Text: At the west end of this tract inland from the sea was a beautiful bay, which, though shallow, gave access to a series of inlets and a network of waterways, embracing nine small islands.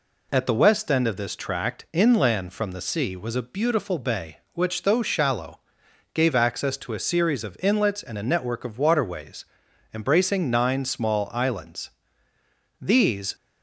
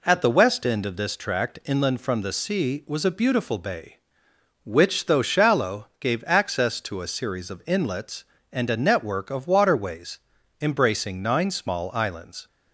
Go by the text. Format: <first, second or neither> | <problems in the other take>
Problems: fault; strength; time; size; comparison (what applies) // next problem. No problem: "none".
second | goes on to say "These"; from 12.7 s on; 0.56 s long